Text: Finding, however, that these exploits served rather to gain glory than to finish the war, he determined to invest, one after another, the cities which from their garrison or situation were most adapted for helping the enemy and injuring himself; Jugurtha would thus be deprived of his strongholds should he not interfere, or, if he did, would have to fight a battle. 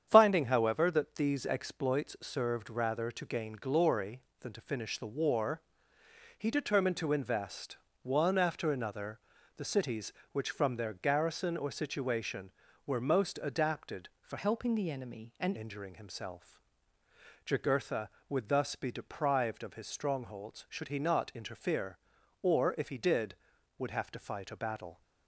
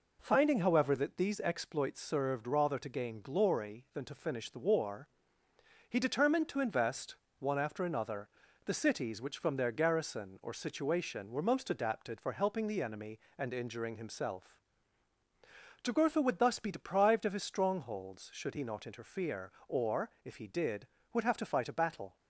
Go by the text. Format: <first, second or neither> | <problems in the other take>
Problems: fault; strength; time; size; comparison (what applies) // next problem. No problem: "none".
second | starts louder than the rest; strong; until 1.0 s; 8.5 dB // changes voice from "helping" to "and"; from 14.3 to 15.5 s; 1.2 s long